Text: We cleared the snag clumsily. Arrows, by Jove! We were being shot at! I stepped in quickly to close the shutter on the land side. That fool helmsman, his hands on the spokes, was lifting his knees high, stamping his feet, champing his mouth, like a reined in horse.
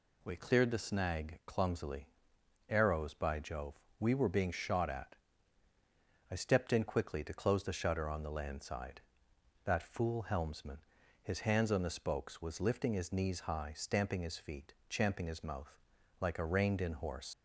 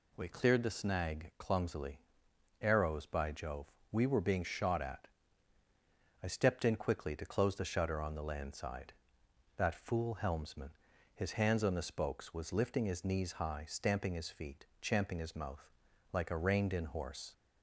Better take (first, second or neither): second